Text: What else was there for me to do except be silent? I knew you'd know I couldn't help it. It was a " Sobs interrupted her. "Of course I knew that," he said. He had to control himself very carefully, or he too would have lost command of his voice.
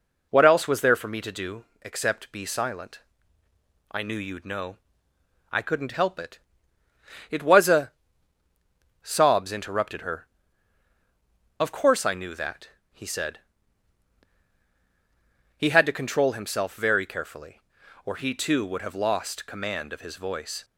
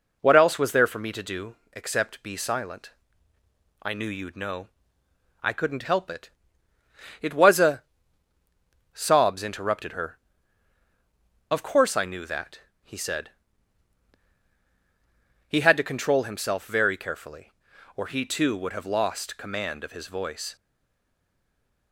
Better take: first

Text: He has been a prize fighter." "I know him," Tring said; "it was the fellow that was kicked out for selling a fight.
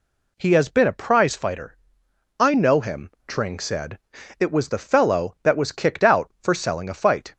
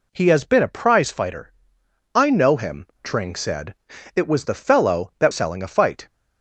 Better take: first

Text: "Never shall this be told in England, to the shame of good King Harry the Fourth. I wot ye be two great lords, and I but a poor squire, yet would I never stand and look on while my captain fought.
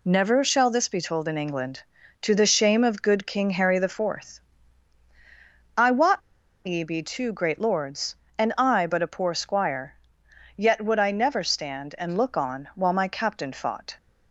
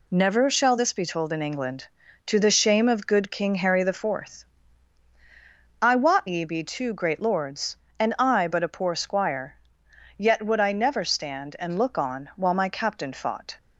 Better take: second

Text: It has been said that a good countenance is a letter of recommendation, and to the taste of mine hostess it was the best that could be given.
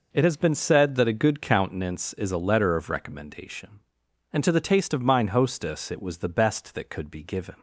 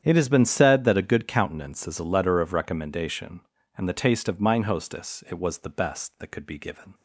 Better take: first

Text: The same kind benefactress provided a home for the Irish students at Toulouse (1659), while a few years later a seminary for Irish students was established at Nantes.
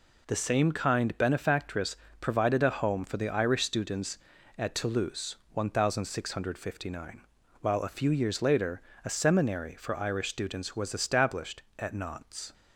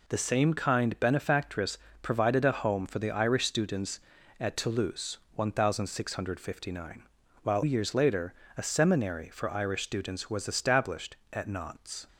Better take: first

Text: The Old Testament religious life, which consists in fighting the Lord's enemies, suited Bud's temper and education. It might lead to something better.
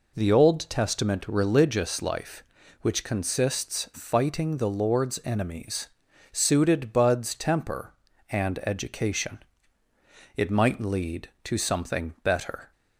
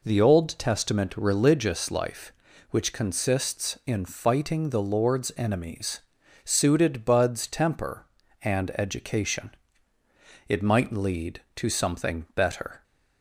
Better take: second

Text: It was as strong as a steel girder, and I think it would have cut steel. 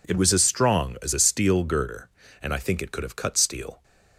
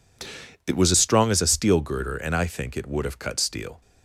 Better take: second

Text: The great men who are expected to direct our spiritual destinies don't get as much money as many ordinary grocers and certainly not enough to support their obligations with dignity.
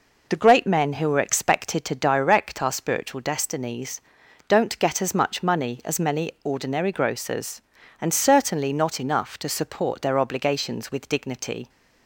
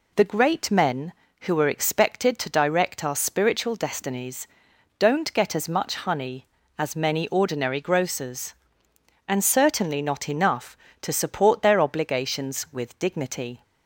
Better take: first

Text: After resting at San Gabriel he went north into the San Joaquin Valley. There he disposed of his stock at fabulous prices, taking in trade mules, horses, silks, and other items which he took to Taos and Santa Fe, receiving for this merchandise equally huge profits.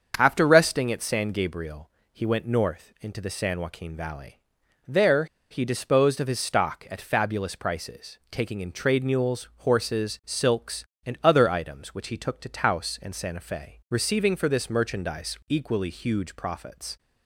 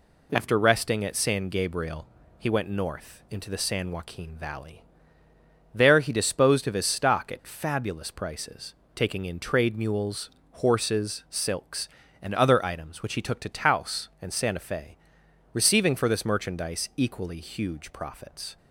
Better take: second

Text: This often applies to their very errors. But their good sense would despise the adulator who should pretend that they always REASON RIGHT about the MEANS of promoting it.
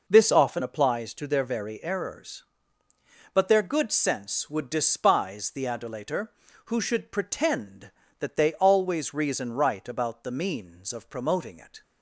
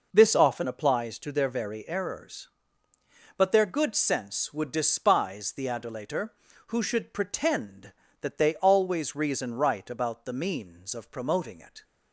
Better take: neither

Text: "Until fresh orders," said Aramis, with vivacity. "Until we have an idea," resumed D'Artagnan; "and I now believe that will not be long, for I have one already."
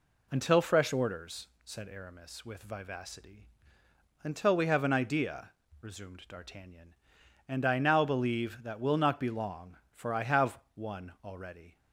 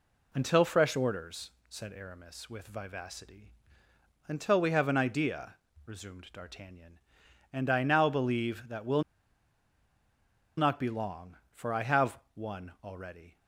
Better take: first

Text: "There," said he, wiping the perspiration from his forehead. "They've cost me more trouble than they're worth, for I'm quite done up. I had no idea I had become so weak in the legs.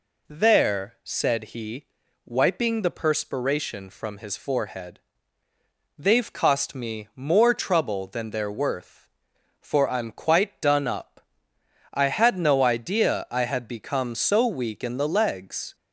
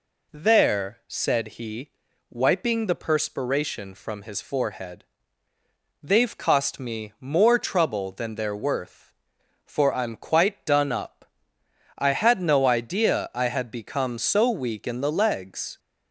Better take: neither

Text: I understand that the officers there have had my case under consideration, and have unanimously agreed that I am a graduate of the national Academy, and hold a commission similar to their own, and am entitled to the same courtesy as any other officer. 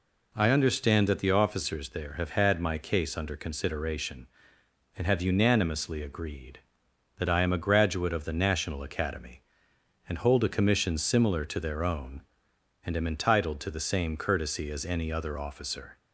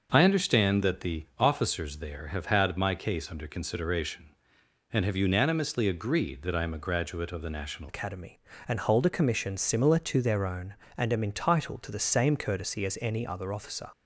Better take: first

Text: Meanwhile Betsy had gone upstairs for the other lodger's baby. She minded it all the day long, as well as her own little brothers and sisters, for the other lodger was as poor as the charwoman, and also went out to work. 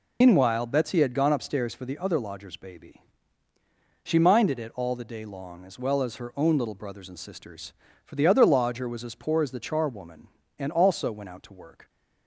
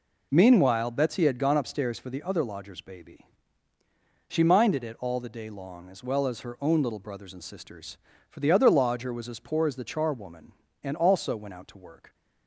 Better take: second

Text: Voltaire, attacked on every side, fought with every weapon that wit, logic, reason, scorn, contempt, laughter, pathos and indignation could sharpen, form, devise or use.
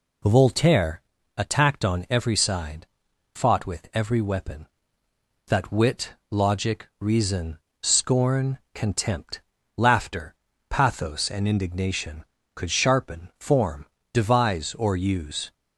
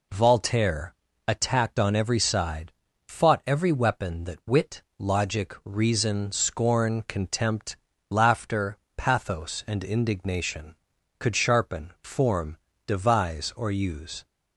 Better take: first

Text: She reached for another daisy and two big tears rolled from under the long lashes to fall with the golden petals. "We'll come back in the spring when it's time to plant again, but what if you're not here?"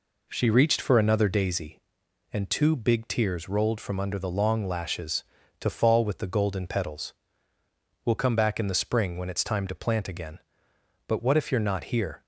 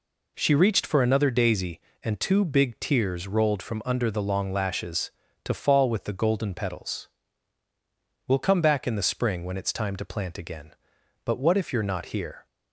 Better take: neither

